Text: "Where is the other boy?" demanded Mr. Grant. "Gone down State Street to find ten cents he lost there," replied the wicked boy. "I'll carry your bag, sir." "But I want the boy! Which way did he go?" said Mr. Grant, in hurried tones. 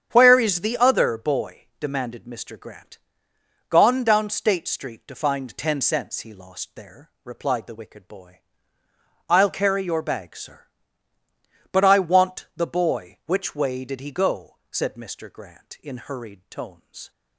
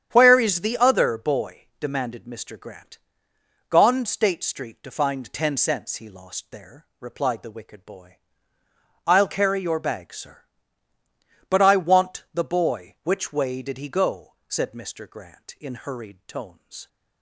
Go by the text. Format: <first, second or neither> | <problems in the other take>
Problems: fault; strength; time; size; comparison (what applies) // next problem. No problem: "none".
first | starts louder than the rest; strong; until 1.1 s; 9 dB; strong in the first // skips "down"; at 4.0 s